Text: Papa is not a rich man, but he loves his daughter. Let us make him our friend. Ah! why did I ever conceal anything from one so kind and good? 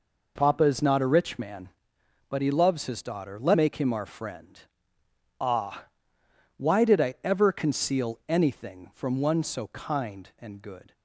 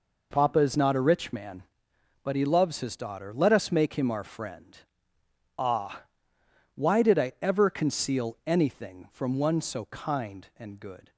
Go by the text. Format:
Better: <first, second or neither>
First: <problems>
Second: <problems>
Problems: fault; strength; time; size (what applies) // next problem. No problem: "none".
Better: second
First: skips "us"; at 3.5 s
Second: none